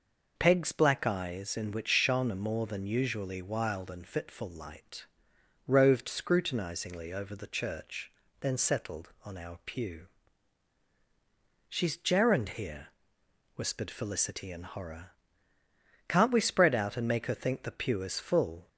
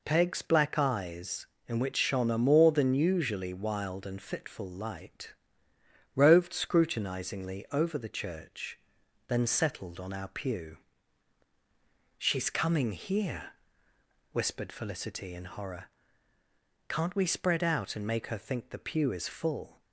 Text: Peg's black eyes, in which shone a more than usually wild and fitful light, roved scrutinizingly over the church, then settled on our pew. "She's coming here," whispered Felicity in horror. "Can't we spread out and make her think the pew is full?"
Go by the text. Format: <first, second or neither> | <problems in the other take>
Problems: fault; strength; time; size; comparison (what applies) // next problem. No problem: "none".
second | says "gerund" for "coming"; at 11.9 s